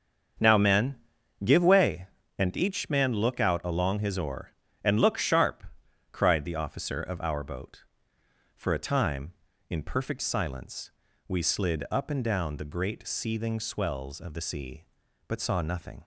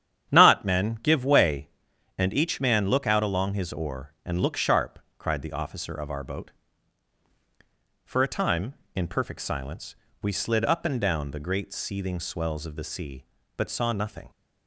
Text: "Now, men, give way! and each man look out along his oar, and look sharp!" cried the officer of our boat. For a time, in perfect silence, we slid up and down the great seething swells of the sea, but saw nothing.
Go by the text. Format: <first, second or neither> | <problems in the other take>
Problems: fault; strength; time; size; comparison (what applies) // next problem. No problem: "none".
first | starts louder than the rest; strong; until 1.3 s; 9.5 dB; strong in the first // says "Not" for "Now"; at 0.3 s